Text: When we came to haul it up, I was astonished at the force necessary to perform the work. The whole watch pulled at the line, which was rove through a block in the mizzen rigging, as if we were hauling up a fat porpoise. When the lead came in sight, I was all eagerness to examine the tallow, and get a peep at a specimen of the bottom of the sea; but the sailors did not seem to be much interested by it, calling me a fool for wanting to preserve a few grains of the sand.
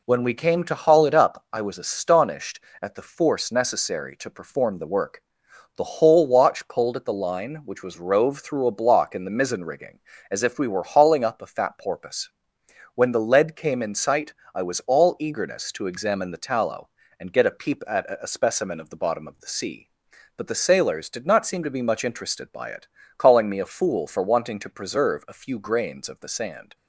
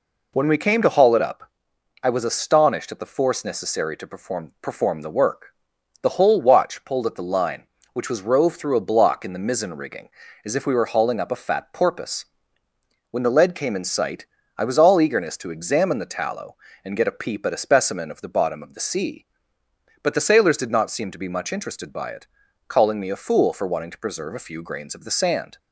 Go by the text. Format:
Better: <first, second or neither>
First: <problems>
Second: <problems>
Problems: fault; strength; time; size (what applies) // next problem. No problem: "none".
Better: first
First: none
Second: says "perform" twice; at 4.6 s